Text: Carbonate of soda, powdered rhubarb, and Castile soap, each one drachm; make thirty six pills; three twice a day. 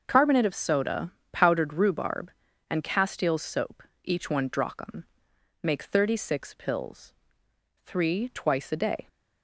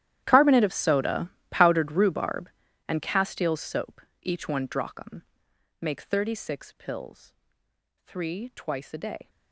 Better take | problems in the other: first | gets quieter; strong; throughout; 18.5 dB // starts louder than the rest; strong; until 1.2 s; 12 dB; also in the first

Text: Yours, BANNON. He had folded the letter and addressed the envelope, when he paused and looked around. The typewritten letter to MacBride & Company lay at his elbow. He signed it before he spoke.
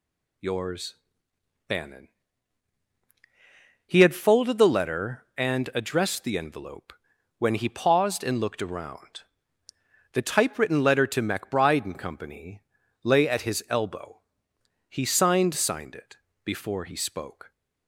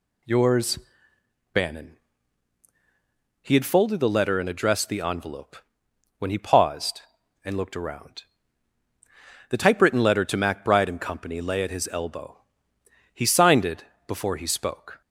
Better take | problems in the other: second | pauses between "Company" and "lay"; at 12.6 s; 0.42 s long // says "signed" twice; at 15.5 s // pauses between "it" and "before"; slight; at 16.1 s; 0.26 s long; slight in the second

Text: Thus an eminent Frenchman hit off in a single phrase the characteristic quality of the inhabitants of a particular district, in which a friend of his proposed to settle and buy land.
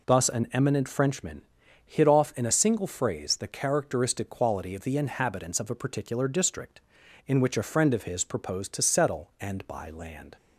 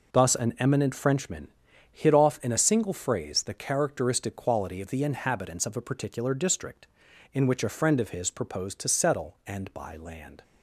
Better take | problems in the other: first | gets quieter; strong; throughout; 10 dB // pauses between "Frenchman" and "hit"; at 1.4 s; 0.42 s long; also in the first

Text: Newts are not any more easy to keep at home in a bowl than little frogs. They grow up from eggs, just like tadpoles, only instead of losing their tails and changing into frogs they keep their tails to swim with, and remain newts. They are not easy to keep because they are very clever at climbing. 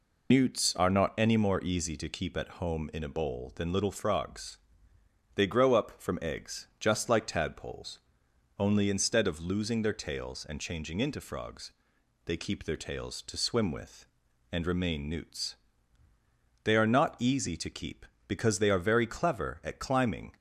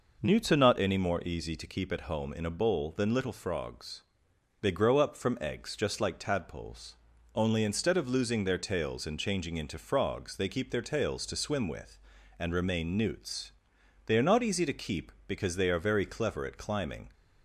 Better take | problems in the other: second | loses the start of "Newts"; at 0.3 s; 110 ms // pauses between "frogs" and "they"; noticeable; at 11.7 s; 0.54 s long

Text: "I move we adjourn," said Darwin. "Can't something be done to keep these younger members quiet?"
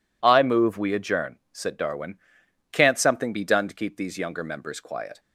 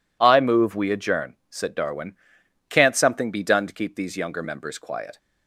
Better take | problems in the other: neither | none

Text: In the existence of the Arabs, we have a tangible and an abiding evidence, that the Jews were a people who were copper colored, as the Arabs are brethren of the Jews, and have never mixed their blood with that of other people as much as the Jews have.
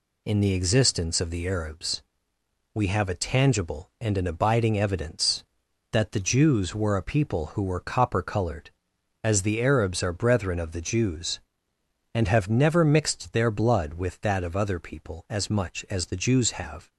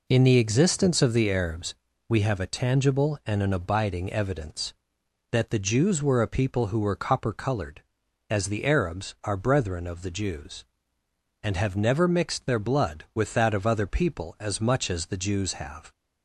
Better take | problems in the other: neither | none

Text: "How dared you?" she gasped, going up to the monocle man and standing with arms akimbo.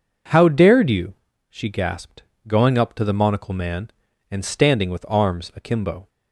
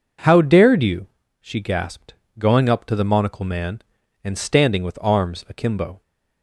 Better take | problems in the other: neither | none

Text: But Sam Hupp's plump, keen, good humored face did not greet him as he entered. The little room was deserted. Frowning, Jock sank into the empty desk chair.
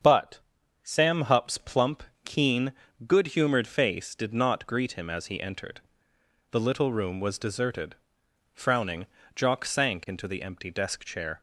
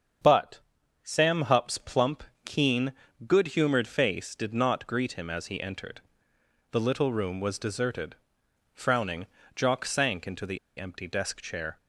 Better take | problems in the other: first | starts louder than the rest; strong; until 1.6 s; 7.5 dB; strong in the first // pauses between "But" and "Sam"; at 0.6 s; 0.42 s long; also in the first // pauses between "the" and "empty"; slight; at 10.5 s; 0.20 s long

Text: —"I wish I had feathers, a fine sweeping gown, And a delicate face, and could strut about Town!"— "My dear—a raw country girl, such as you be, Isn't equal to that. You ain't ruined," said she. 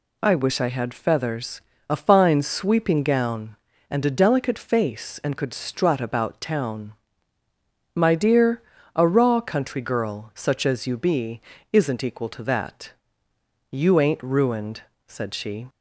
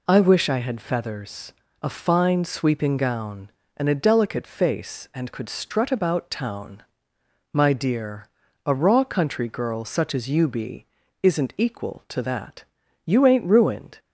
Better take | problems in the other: first | stops before "said she"; at 13.9 s

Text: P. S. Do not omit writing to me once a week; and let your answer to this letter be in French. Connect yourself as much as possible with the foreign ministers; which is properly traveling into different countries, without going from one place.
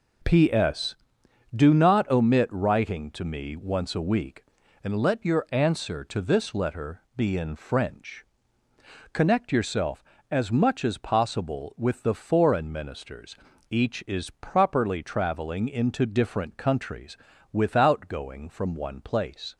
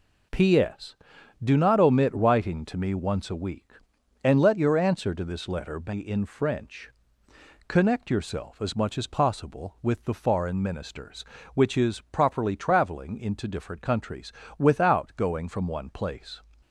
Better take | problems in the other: second | pauses between "letter" and "be"; slight; at 7.0 s; 0.16 s long // says "each" for "which"; at 13.6 s

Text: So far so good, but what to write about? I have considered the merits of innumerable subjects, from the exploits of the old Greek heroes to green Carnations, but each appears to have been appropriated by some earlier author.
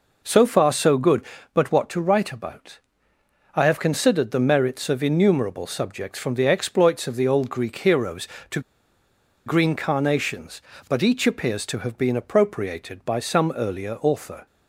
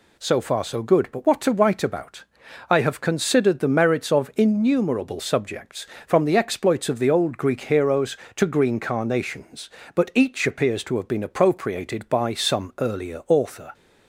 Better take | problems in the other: second | pauses between "to" and "green"; noticeable; at 8.5 s; 0.86 s long

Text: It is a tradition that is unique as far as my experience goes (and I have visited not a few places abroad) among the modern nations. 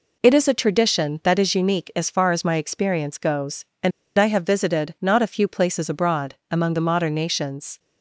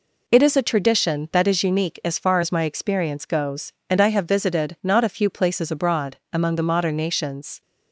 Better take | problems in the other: second | pauses between "and" and "I"; slight; at 3.9 s; 0.27 s long

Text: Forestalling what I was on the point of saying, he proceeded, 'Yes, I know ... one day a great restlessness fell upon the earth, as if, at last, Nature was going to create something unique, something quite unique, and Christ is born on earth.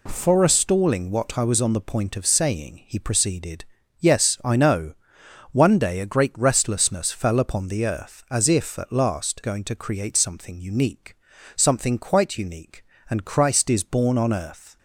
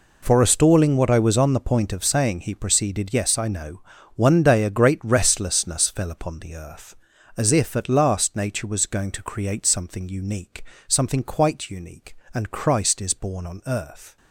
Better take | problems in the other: second | skips "Nature was"; at 9.4 s

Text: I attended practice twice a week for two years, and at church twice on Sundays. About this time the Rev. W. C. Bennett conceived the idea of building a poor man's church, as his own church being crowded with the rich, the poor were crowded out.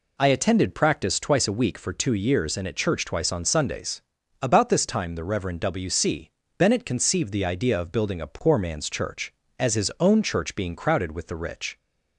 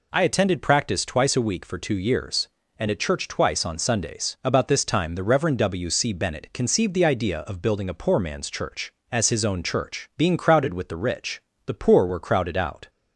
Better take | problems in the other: second | pauses between "C" and "Bennett"; slight; at 6.3 s; 0.26 s long // stops before "the poor were crowded out"; at 11.7 s

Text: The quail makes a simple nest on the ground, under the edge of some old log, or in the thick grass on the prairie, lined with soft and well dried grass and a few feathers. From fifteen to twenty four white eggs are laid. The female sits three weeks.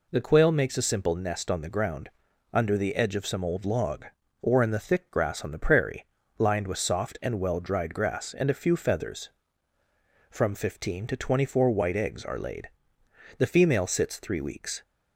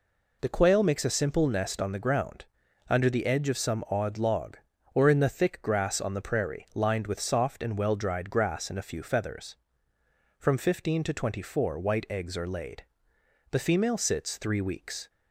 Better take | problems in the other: first | says "odd" for "old"; at 3.9 s

